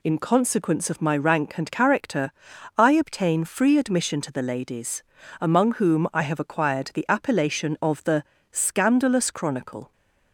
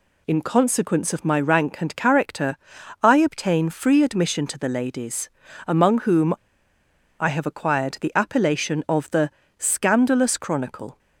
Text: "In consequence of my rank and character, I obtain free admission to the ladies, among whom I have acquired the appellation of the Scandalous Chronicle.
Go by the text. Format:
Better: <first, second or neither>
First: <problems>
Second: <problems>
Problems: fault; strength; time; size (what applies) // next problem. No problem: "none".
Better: first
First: pauses between "the" and "Scandalous"; slight; at 8.2 s; 0.28 s long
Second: pauses between "whom" and "I"; noticeable; at 6.3 s; 0.86 s long // pauses between "the" and "Scandalous"; slight; at 9.3 s; 0.28 s long